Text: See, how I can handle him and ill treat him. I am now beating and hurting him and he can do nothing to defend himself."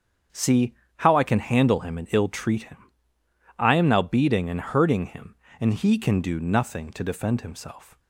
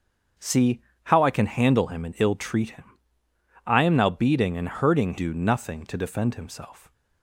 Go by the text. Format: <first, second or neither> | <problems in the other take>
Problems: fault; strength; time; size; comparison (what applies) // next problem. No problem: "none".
first | starts louder than the rest; until 1.6 s; 7 dB; strong in the first // skips "him and he can"; at 5.1 s